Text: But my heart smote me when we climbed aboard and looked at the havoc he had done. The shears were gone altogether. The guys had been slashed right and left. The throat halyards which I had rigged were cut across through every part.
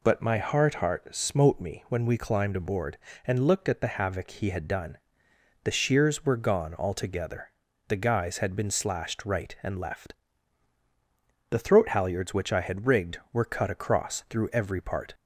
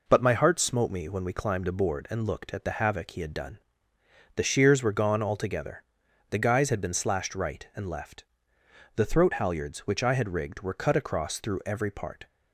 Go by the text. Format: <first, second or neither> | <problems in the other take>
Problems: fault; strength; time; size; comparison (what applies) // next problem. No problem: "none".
second | says "heart" twice; at 0.7 s